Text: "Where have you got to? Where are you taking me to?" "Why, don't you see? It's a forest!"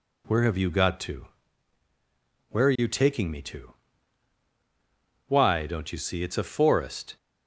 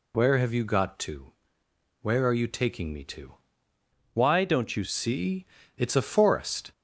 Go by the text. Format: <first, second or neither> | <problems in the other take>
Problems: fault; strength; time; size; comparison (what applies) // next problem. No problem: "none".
first | changes voice from "Why" to "you"; from 4.1 to 4.8 s; 0.7 s long